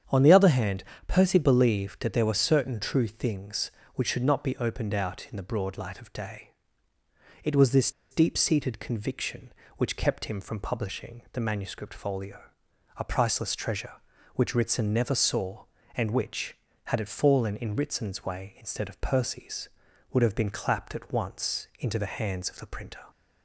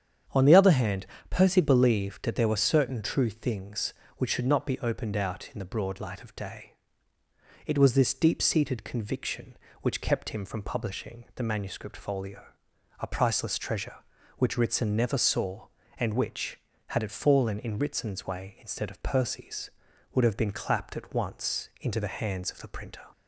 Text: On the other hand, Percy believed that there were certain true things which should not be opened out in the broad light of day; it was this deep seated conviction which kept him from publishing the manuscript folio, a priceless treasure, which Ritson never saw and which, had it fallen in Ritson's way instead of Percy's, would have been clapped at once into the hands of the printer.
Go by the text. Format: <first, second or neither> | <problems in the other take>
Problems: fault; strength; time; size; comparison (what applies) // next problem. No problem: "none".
second | starts louder than the rest; strong; until 1.3 s; 8 dB; strong in the second // pauses between "this" and "deep"; slight; at 7.9 s; 0.20 s long